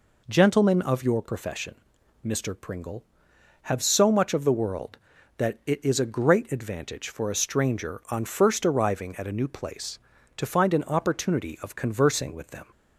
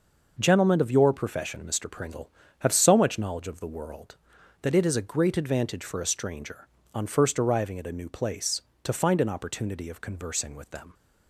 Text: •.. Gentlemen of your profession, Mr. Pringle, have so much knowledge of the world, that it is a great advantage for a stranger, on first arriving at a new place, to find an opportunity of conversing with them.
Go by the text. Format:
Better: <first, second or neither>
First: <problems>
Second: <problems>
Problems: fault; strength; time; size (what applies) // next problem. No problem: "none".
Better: second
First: skips "knowledge"; at 4.3 s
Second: none